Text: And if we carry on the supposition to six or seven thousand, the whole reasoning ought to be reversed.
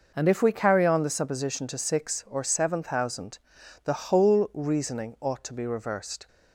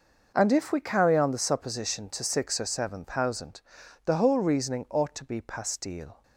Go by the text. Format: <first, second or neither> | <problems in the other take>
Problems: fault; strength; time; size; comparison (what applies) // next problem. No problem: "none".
first | says "pastille" for "reversed"; at 5.4 s